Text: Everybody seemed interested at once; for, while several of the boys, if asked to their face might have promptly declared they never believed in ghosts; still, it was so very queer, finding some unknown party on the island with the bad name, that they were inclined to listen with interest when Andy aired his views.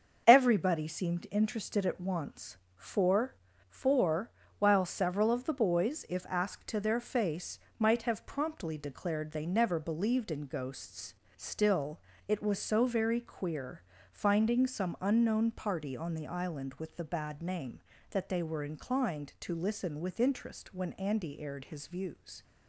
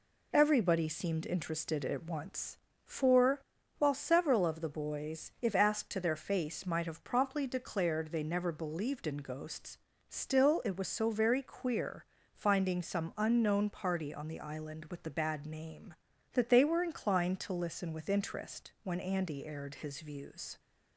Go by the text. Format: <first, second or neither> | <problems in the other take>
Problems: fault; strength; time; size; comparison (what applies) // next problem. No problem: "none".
second | starts louder than the rest; until 1.2 s; 6.5 dB // says "for" twice; at 3.6 s // pauses between "face" and "might"; slight; at 7.5 s; 0.22 s long